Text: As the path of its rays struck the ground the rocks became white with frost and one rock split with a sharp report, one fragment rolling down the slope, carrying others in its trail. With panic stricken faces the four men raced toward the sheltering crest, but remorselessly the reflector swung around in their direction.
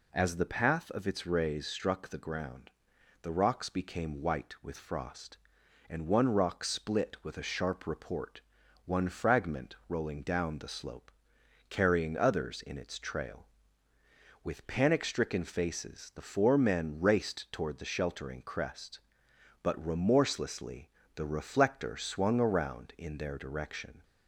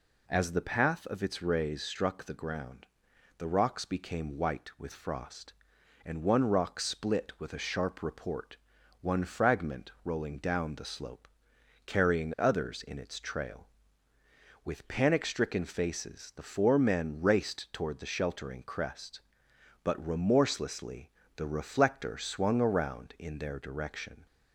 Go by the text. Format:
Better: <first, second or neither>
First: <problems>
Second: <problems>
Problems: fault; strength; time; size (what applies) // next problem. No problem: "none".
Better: neither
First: pauses between "ground" and "the"; noticeable; at 2.7 s; 0.50 s long // pauses between "remorselessly" and "the"; slight; at 20.8 s; 0.26 s long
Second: pauses between "ground" and "the"; noticeable; at 2.8 s; 0.50 s long // pauses between "remorselessly" and "the"; slight; at 21.0 s; 0.26 s long